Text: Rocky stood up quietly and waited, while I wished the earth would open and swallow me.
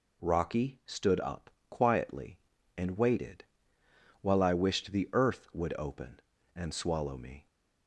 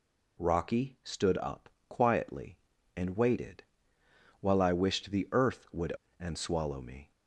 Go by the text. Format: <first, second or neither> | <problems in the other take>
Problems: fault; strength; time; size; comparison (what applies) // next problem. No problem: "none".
first | pauses between "up" and "quietly"; slight; at 1.6 s; 0.22 s long; slight in the first // skips "open"; at 6.0 s